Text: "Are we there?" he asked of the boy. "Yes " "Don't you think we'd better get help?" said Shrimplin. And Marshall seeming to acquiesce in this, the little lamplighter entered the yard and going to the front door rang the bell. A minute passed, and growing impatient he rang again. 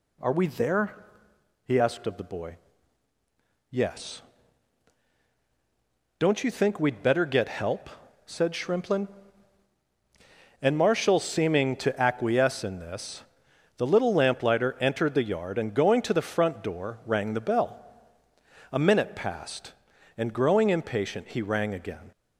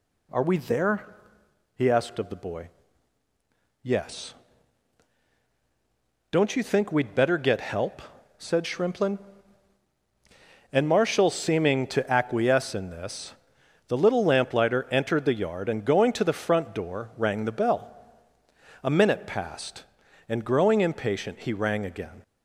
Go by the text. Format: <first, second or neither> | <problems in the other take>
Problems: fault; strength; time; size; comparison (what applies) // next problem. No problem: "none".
neither | none